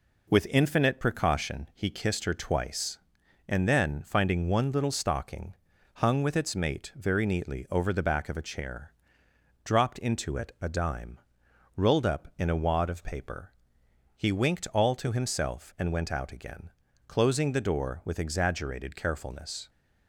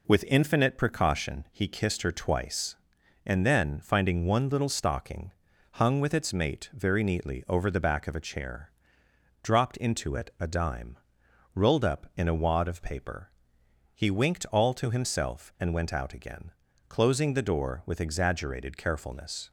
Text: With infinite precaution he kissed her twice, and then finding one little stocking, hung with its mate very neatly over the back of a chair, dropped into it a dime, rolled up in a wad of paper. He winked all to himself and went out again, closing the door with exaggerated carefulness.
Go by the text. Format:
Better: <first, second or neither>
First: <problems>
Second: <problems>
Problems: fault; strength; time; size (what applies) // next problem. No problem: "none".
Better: neither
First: none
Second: none